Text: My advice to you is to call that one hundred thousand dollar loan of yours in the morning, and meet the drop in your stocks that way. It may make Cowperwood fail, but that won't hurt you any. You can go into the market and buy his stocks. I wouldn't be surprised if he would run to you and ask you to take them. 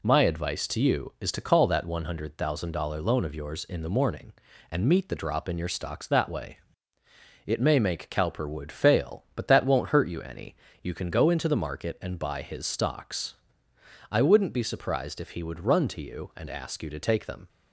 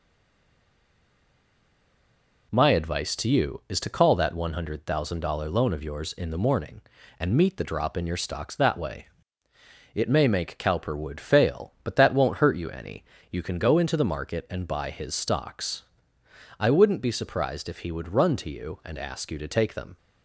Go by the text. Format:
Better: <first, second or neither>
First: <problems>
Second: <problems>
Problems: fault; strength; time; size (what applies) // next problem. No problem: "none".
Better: first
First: none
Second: stays silent before the first word; until 2.5 s; 2.5 s long